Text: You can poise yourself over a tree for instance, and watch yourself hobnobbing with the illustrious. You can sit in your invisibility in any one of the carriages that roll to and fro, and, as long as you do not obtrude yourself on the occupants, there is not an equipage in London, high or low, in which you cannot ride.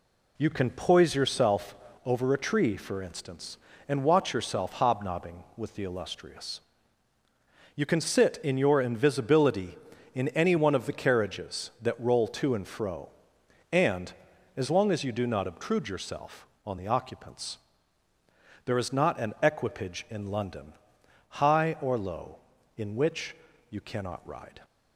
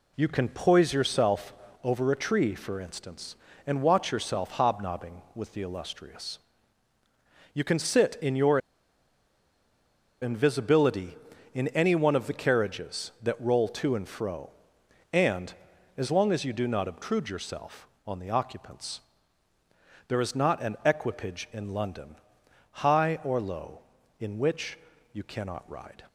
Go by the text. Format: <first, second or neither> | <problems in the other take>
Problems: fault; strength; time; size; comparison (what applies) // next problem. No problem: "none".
first | pauses between "yourself" and "over"; slight; at 1.5 s; 0.28 s long; slight in the first // pauses between "your" and "invisibility"; strong; at 8.5 s; 1.6 s long // pauses between "which" and "you"; slight; at 24.7 s; 0.36 s long; slight in the first